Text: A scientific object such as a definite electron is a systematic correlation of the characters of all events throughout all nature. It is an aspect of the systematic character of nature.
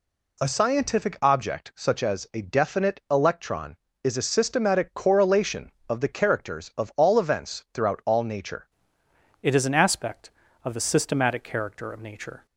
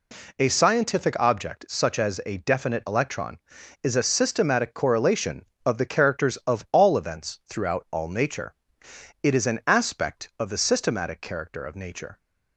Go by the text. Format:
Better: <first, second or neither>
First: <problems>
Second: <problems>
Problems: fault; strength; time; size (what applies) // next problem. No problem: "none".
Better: second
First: changes voice at "It"; from 9.4 s on; 3.0 s long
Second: none